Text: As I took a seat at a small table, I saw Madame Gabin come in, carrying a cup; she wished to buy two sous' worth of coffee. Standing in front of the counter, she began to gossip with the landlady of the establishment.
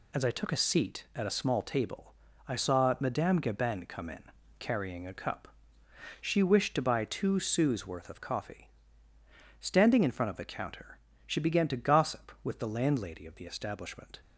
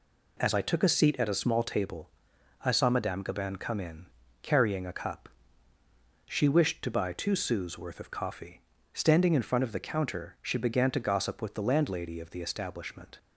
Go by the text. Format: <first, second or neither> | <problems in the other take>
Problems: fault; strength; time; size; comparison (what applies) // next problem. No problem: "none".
neither | none